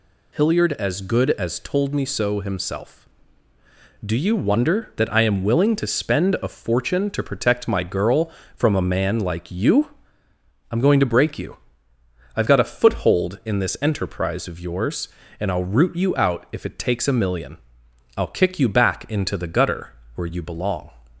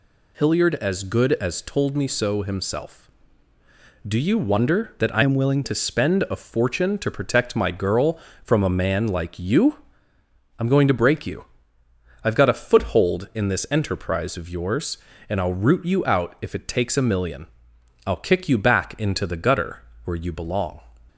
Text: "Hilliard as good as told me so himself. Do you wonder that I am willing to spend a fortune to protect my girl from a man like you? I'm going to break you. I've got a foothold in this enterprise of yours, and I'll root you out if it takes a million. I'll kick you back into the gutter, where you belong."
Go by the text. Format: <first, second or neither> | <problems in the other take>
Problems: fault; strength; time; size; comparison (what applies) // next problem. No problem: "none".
first | changes voice from "am" to "willing"; from 5.2 to 5.6 s; 0.4 s long